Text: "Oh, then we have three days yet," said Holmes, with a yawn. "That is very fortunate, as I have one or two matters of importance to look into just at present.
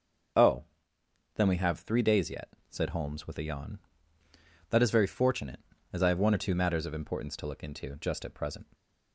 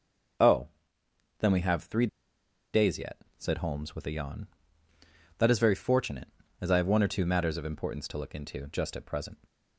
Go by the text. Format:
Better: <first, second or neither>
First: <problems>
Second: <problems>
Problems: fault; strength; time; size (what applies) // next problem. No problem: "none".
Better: first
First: starts louder than the rest; until 2.0 s; 6.5 dB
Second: starts louder than the rest; until 2.8 s; 6.5 dB // pauses between "three" and "days"; noticeable; at 2.0 s; 0.66 s long